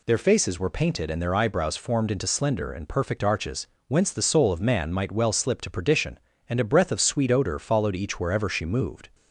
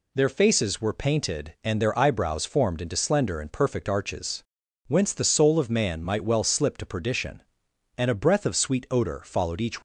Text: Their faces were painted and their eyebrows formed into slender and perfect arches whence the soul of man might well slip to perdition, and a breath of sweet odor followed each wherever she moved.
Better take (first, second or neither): first